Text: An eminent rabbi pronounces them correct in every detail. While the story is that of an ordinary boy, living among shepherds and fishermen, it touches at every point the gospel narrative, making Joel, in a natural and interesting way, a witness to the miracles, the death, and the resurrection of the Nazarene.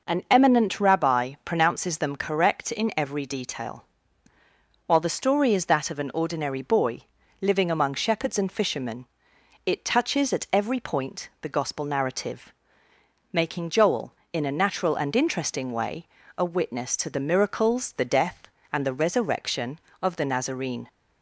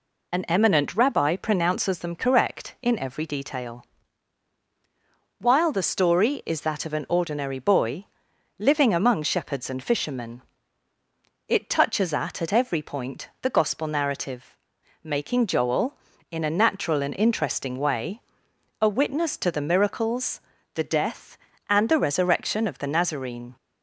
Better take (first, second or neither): first